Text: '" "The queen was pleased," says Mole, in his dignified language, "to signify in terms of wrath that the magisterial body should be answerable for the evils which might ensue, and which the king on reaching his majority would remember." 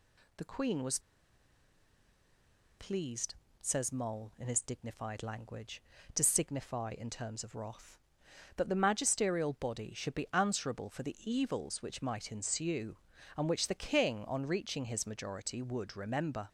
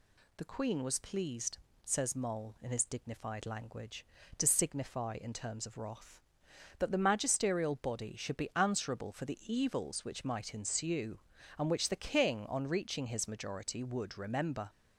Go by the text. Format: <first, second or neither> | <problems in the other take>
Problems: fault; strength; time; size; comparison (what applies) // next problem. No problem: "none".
second | pauses between "was" and "pleased"; strong; at 0.9 s; 1.7 s long